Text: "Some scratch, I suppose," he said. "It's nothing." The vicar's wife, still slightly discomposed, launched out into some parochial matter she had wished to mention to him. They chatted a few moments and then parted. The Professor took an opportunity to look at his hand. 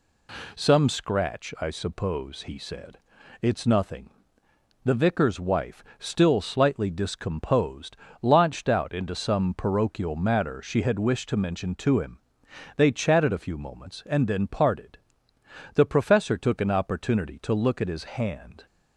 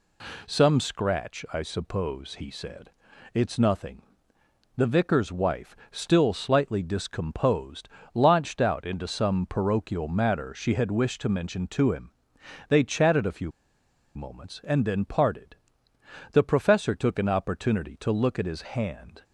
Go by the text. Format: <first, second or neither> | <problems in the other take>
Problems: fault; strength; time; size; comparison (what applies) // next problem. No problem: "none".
first | pauses between "few" and "moments"; noticeable; at 13.5 s; 0.64 s long